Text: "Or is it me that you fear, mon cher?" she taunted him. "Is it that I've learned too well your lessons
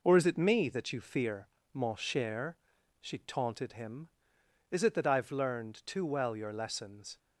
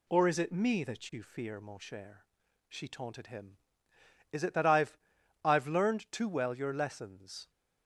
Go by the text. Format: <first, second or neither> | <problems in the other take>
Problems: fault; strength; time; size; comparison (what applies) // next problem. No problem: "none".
first | says "I've" twice; at 5.4 s